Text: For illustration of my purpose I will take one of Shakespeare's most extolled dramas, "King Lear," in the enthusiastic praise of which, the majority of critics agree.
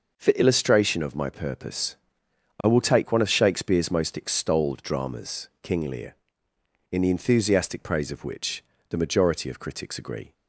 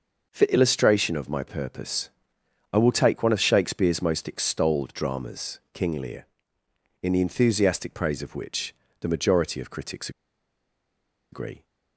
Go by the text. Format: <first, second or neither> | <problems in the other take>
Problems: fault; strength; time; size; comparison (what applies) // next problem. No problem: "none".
first | pauses between "purpose" and "I"; noticeable; at 2.1 s; 0.62 s long; noticeable in the first // pauses between "critics" and "agree"; at 10.1 s; 1.2 s long